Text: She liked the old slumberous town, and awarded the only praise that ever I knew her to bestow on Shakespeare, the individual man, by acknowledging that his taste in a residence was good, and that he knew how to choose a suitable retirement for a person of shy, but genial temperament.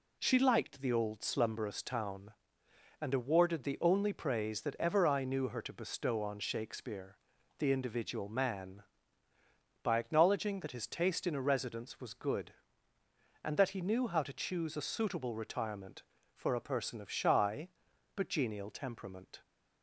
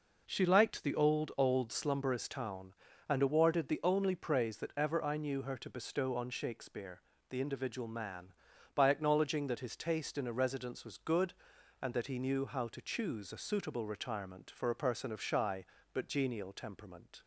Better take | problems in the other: first | says "old" twice; at 1.3 s

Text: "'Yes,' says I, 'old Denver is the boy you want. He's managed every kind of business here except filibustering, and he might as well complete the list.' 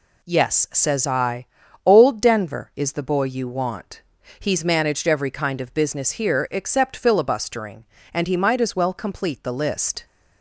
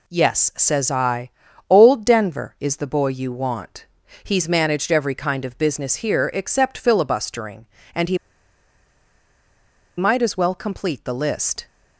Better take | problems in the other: first | pauses between "he" and "might"; strong; at 8.1 s; 1.8 s long

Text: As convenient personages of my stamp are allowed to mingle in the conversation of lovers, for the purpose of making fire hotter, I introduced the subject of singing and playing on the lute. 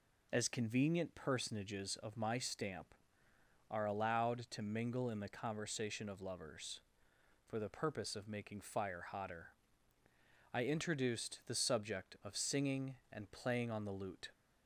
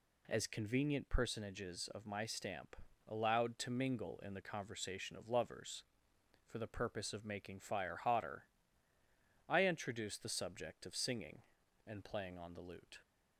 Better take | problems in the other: first | skips "are"; at 2.8 s

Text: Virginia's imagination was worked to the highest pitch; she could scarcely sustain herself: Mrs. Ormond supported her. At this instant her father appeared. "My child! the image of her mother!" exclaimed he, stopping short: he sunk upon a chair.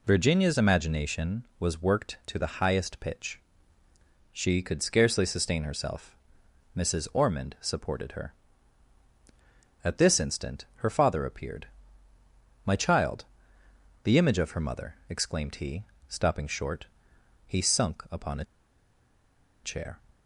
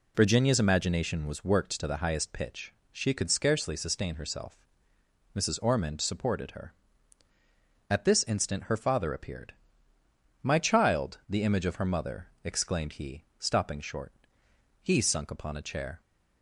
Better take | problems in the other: second | pauses between "a" and "chair"; at 18.4 s; 1.1 s long

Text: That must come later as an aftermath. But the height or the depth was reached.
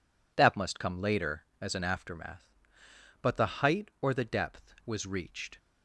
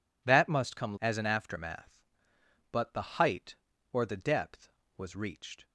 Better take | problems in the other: first | skips "later"; at 0.9 s

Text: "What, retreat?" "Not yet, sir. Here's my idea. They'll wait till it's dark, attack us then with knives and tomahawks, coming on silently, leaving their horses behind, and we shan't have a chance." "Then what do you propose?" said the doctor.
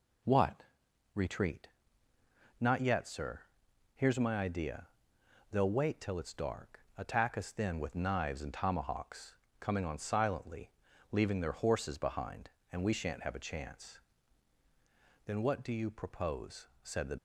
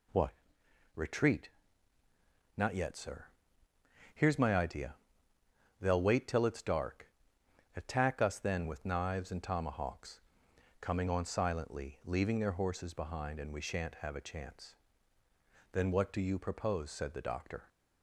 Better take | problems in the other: second | stops before "doctor"; at 17.1 s

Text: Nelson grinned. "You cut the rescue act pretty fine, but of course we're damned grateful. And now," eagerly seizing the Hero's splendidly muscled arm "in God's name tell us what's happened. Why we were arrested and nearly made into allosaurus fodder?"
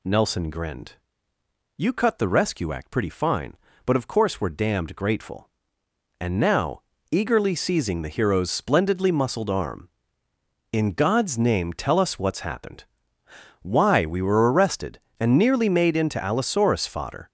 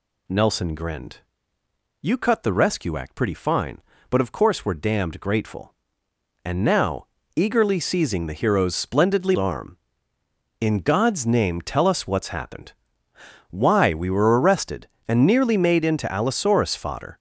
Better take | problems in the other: first | skips "muscled"; at 9.3 s

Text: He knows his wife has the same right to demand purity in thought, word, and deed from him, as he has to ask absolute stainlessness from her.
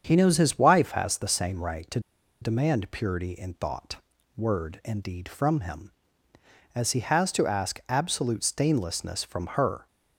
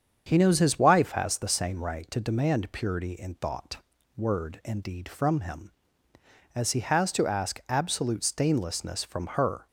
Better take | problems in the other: second | starts louder than the rest; strong; until 1.0 s; 7.5 dB; strong in the second // pauses between "to" and "demand"; at 1.9 s; 0.42 s long

